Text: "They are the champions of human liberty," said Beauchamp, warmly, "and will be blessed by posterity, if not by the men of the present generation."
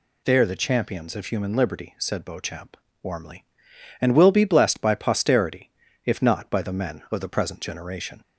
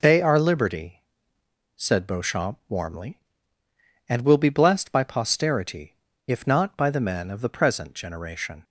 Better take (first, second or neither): first